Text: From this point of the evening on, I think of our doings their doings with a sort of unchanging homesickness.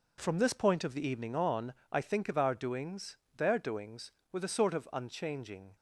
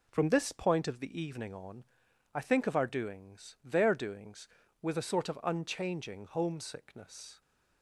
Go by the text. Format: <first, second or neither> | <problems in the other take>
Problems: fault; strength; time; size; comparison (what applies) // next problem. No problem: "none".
second | pauses between "doings" and "their"; slight; at 3.1 s; 0.22 s long // stops before "homesickness"; at 5.7 s